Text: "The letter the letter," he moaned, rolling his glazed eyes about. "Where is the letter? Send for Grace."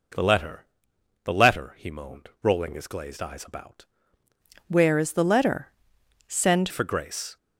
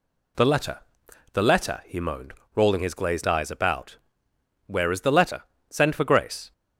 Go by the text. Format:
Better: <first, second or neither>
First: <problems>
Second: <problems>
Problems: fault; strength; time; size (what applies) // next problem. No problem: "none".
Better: second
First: pauses between "letter" and "the"; noticeable; at 0.6 s; 0.56 s long // changes voice from "Where" to "Send"; from 4.6 to 6.6 s; 2.0 s long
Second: pauses between "letter" and "the"; noticeable; at 0.8 s; 0.50 s long